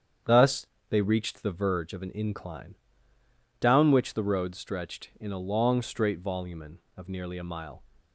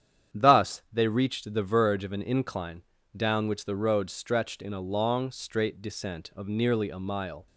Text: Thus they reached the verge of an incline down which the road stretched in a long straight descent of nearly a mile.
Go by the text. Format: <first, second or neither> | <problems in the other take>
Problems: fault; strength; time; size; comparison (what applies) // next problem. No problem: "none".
second | starts louder than the rest; strong; until 1.5 s; 8.5 dB; strong in the second // pauses between "Thus" and "they"; slight; at 0.6 s; 0.24 s long // pauses between "incline" and "down"; noticeable; at 2.7 s; 0.86 s long; slight in the second // says "volumen" for "descent"; at 6.1 s